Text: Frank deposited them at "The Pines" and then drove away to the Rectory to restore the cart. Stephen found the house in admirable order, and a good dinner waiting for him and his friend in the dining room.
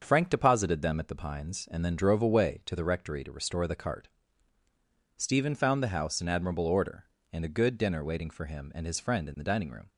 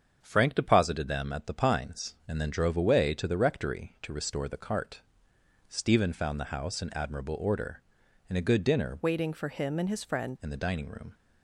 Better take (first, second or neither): first